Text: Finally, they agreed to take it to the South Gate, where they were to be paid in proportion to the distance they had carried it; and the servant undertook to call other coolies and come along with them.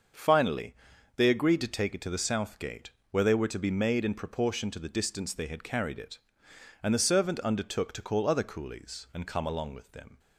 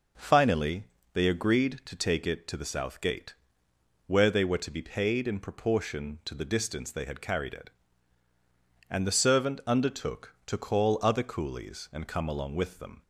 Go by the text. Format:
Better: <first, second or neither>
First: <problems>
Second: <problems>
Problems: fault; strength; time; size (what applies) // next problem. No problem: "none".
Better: second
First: starts louder than the rest; until 1.6 s; 6.5 dB // says "made" for "paid"; at 3.6 s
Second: none